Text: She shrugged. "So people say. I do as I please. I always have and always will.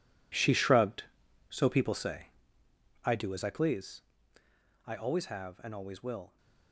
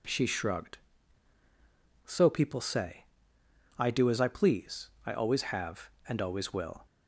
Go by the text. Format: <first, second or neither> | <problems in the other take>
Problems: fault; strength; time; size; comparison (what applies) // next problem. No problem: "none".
second | gets quieter; strong; throughout; 13 dB